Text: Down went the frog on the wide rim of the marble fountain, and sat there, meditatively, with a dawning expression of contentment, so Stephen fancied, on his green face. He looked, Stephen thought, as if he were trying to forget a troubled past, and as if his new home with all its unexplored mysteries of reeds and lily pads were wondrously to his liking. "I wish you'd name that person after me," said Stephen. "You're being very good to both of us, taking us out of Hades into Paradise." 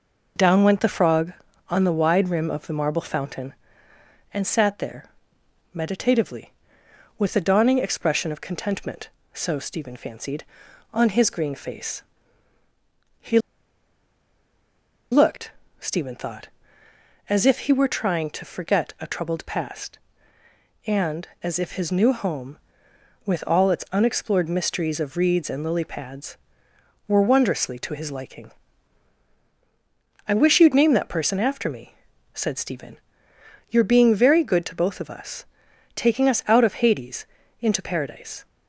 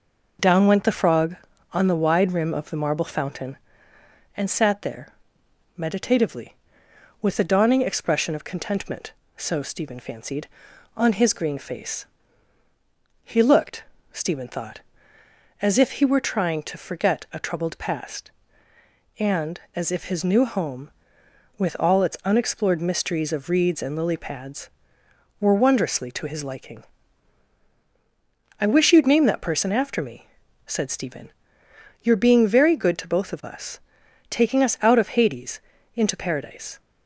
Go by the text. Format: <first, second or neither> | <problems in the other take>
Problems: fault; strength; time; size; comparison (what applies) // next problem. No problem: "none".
second | pauses between "He" and "looked"; strong; at 13.3 s; 1.7 s long // pauses between "Hades" and "into"; slight; at 37.2 s; 0.34 s long; slight in the second